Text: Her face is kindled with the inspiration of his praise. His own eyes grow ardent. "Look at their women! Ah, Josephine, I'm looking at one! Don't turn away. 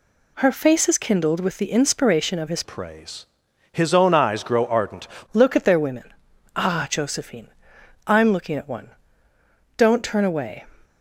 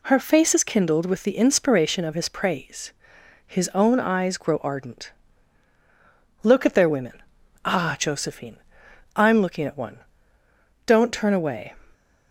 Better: second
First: changes voice from "praise" to "ardent"; from 2.6 to 5.0 s; 2.4 s long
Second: none

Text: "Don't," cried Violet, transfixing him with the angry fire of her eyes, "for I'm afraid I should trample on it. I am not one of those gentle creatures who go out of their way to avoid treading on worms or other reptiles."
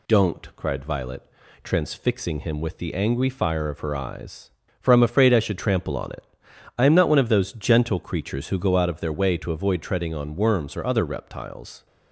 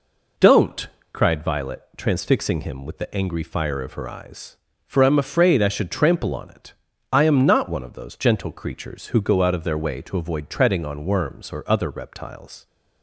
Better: neither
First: none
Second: none

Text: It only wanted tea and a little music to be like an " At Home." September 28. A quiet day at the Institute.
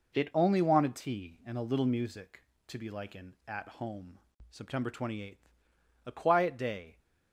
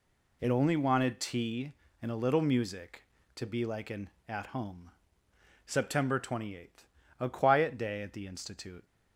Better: second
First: stops before "at the Institute"; at 6.9 s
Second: none

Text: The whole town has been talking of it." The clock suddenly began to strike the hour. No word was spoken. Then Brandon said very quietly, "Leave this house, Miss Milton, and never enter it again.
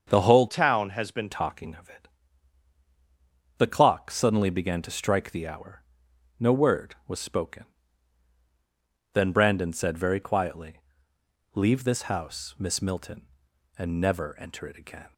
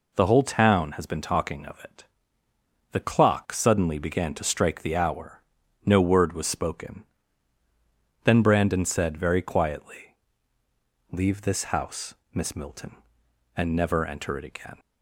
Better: second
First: starts louder than the rest; until 1.0 s; 6.5 dB // changes voice from "town" to "been"; from 0.4 to 1.3 s; 0.9 s long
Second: none

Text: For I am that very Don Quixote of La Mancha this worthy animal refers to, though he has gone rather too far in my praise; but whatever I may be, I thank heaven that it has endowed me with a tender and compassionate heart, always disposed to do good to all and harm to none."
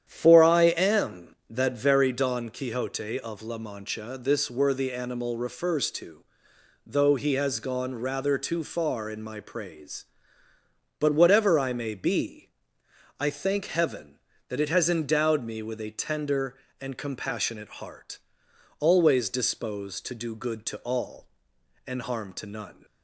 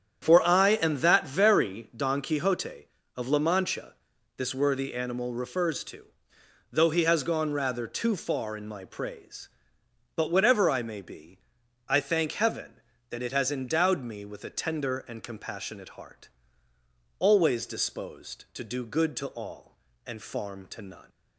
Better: first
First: starts louder than the rest; strong; until 1.0 s; 9.5 dB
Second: starts louder than the rest; strong; until 1.2 s; 8.5 dB // pauses between "Mancha" and "this"; at 3.9 s; 0.42 s long // says "farm" for "harm"; at 20.2 s

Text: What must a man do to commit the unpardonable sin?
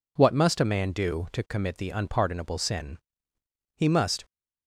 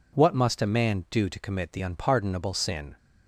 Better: second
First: goes on to say "He must"; slight; from 3.7 s on; 0.48 s long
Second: none

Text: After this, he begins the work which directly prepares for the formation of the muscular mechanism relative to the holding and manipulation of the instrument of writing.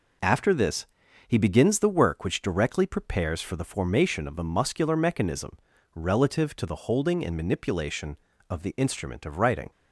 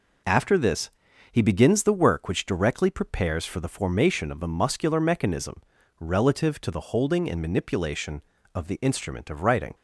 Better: neither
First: pauses between "mechanism" and "relative"; at 5.5 s; 0.37 s long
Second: pauses between "mechanism" and "relative"; at 5.6 s; 0.38 s long

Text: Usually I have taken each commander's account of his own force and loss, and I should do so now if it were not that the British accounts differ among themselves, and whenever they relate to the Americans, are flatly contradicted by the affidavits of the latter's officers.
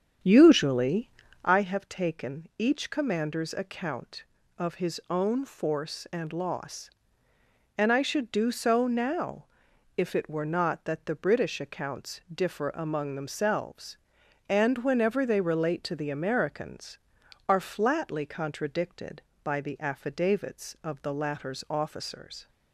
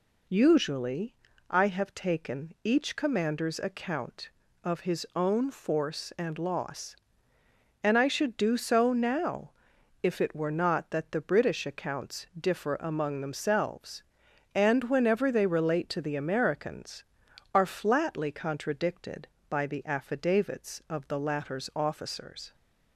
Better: second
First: starts louder than the rest; strong; until 1.6 s; 8.5 dB // pauses between "Usually" and "I"; slight; at 1.0 s; 0.36 s long // pauses between "now" and "if"; noticeable; at 9.4 s; 0.50 s long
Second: pauses between "Usually" and "I"; slight; at 1.1 s; 0.36 s long // pauses between "now" and "if"; noticeable; at 9.5 s; 0.50 s long

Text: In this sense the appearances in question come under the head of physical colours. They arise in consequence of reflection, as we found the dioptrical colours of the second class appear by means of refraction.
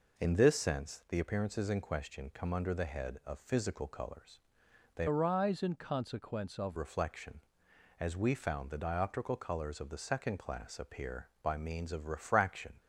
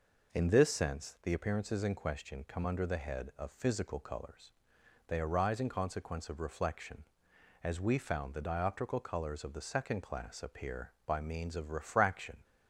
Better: second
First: changes voice from "arise" to "of"; from 5.0 to 6.7 s; 1.7 s long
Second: none

